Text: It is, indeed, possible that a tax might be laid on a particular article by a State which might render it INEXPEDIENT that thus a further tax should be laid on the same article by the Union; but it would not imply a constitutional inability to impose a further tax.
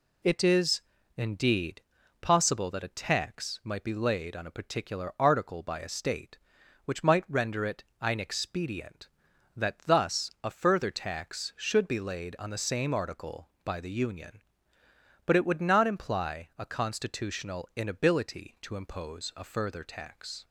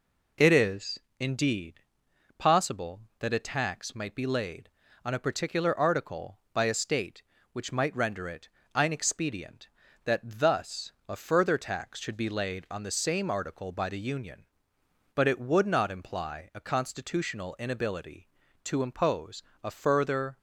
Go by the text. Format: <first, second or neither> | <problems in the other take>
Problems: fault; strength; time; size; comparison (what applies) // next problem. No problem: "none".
first | pauses between "it" and "INEXPEDIENT"; slight; at 8.4 s; 0.26 s long; slight in the first // pauses between "thus" and "a"; slight; at 10.9 s; 0.16 s long // pauses between "impose" and "a"; slight; at 19.4 s; 0.22 s long // stops before "tax"; at 20.3 s